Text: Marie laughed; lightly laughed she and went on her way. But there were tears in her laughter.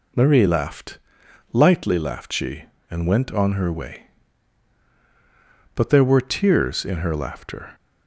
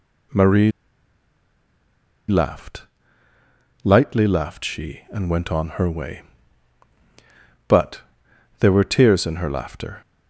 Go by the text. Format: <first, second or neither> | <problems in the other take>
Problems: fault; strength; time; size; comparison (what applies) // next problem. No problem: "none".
first | pauses between "Marie" and "laughed"; strong; at 0.6 s; 1.5 s long // pauses between "But" and "there"; noticeable; at 8.0 s; 0.58 s long